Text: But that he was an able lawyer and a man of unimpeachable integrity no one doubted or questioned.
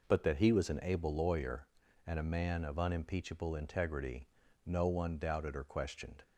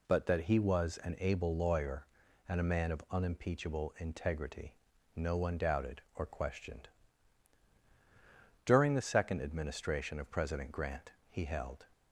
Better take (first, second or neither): first